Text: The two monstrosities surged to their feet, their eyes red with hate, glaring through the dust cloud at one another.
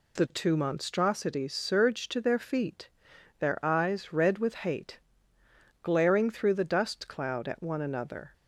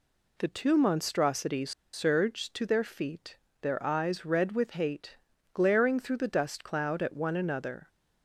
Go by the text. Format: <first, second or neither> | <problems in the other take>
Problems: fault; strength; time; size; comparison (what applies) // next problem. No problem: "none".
first | pauses between "monstrosities" and "surged"; slight; at 1.7 s; 0.22 s long